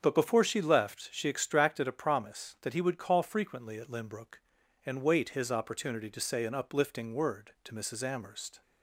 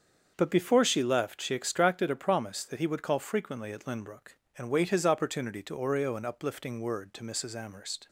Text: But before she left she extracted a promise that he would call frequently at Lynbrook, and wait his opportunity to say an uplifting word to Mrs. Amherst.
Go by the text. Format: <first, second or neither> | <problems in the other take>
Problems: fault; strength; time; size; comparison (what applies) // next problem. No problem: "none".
first | starts louder than the rest; until 1.3 s; 7 dB; also in the first // says "oreo" for "say"; at 5.7 s